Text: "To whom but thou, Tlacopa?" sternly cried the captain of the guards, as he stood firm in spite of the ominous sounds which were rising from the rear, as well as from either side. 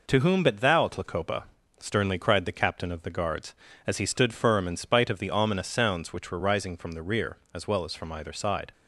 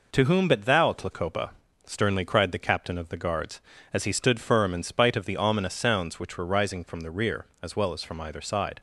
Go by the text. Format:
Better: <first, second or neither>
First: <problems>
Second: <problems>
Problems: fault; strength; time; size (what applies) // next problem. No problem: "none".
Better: neither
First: none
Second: none